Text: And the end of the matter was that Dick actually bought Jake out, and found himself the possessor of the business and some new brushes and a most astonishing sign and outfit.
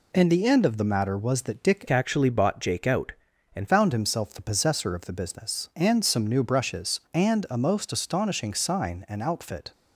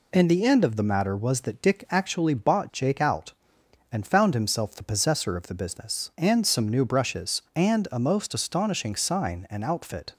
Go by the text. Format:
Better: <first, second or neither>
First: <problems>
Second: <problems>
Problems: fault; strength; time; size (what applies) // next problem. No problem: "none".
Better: second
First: changes voice from "actually" to "and"; from 1.8 to 3.6 s; 1.8 s long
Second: none